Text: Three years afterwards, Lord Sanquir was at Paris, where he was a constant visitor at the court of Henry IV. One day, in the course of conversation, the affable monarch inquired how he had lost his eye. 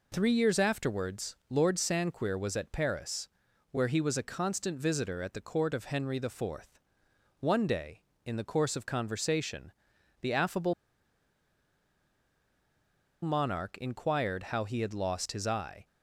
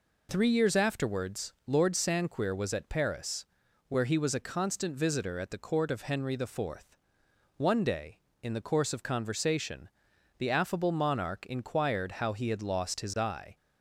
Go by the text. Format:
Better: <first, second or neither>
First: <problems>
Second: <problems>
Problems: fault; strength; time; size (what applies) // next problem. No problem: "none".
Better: second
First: pauses between "affable" and "monarch"; strong; at 10.7 s; 2.5 s long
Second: none